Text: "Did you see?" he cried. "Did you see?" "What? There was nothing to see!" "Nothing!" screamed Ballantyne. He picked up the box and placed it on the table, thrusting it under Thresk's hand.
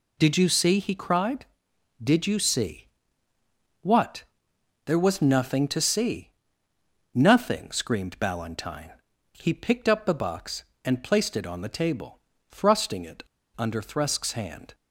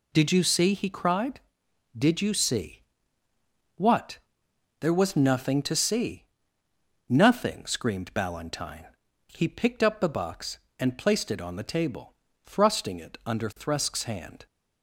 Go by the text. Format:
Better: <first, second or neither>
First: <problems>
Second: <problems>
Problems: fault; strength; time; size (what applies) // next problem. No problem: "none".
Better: second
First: pauses between "it" and "under"; slight; at 13.2 s; 0.34 s long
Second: none